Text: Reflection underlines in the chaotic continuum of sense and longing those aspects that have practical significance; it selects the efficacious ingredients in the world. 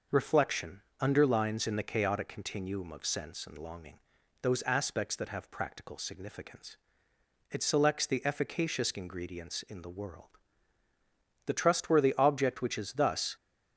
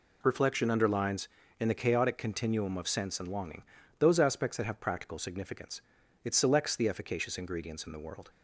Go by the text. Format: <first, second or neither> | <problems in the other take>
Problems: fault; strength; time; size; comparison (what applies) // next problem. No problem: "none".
second | pauses between "Reflection" and "underlines"; slight; at 0.8 s; 0.20 s long // pauses between "longing" and "those"; at 3.9 s; 0.42 s long; also in the second // goes on to say "The trustworthy object which is thus"; strong; from 11.4 s on; 1.9 s long